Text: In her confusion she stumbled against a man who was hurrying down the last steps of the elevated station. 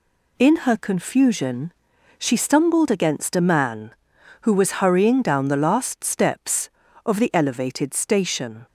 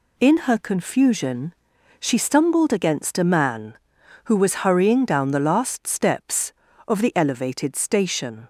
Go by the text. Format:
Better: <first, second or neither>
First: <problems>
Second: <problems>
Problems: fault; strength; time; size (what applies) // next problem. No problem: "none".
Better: neither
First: pauses between "confusion" and "she"; noticeable; at 1.7 s; 0.48 s long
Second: pauses between "confusion" and "she"; noticeable; at 1.5 s; 0.48 s long